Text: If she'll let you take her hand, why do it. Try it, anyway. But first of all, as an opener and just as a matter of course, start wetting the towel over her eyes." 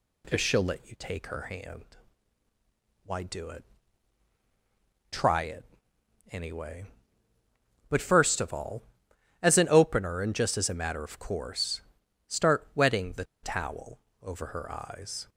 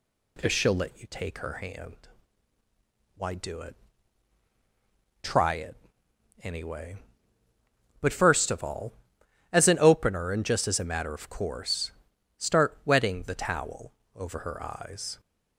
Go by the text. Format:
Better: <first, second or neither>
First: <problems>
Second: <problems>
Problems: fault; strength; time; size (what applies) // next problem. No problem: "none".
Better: second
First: pauses between "the" and "towel"; slight; at 13.2 s; 0.19 s long // pauses between "towel" and "over"; slight; at 13.9 s; 0.22 s long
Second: pauses between "towel" and "over"; slight; at 13.9 s; 0.22 s long